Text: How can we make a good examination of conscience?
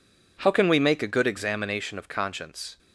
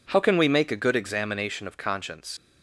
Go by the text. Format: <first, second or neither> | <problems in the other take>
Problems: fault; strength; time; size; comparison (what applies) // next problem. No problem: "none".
first | leaves "conscience" unfinished; at 2.3 s; 100 ms